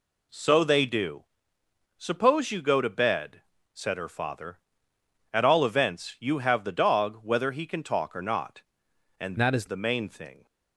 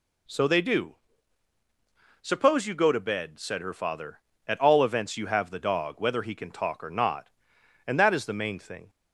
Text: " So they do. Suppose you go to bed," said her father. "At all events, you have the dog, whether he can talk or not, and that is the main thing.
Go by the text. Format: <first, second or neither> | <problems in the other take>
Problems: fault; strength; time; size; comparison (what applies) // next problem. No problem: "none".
second | changes voice from "that" to "is"; from 9.3 to 9.6 s; 0.3 s long